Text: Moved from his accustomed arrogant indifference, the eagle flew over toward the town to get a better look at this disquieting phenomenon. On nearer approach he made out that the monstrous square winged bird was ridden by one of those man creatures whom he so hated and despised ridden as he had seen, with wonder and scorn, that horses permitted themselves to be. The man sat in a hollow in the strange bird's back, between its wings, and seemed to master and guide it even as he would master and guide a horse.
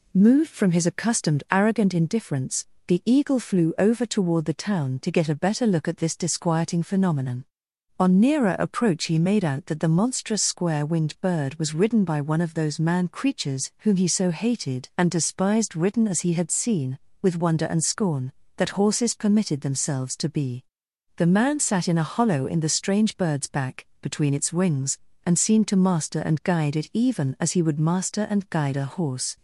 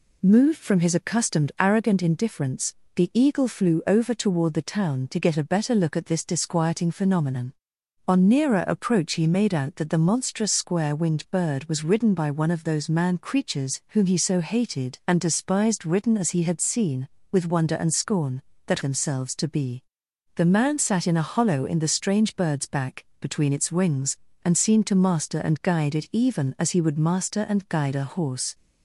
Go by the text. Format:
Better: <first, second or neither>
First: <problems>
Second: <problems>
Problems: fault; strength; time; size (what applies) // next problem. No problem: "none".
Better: first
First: none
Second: skips "horses permitted"; at 18.8 s